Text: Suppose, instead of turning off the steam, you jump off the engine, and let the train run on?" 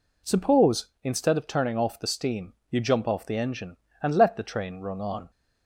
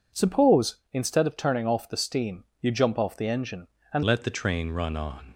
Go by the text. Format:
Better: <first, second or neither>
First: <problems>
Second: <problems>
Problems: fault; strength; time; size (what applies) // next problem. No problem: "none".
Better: first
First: none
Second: changes voice at "let"; from 4.0 s on; 1.3 s long